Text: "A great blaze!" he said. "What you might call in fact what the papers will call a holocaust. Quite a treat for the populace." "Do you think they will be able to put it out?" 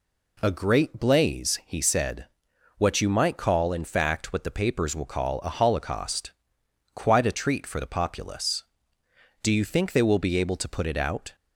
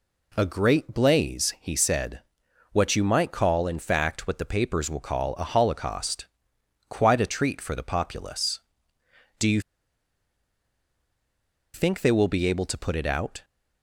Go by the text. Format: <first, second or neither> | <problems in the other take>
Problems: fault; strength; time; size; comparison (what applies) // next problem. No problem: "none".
first | pauses between "you" and "think"; strong; at 9.6 s; 2.1 s long